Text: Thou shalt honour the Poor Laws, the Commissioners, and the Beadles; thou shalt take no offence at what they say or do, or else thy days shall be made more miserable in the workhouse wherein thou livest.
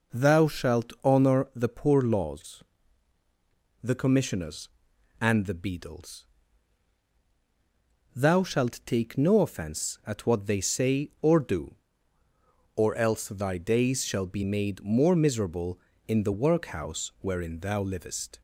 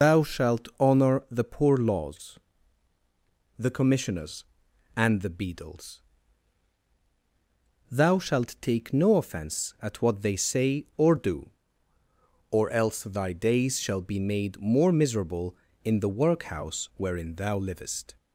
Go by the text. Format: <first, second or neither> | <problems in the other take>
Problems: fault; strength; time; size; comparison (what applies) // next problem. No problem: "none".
first | loses the start of "Thou"; at 0.0 s; 135 ms